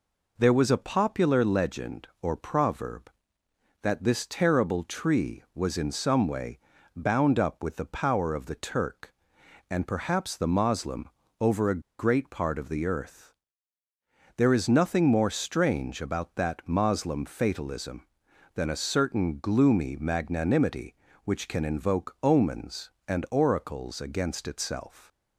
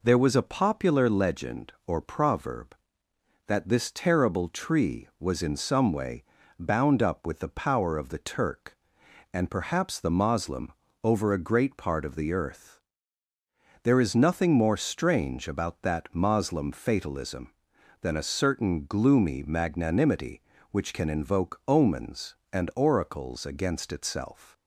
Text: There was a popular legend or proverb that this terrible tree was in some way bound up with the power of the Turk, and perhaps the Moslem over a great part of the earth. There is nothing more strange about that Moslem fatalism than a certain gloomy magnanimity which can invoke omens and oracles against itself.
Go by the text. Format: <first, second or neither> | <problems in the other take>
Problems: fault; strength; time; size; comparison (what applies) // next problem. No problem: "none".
second | pauses between "way" and "bound"; slight; at 6.5 s; 0.34 s long; slight in the second // pauses between "Moslem" and "over"; slight; at 11.0 s; 0.32 s long; slight in the second // pauses between "a" and "great"; slight; at 11.7 s; 0.19 s long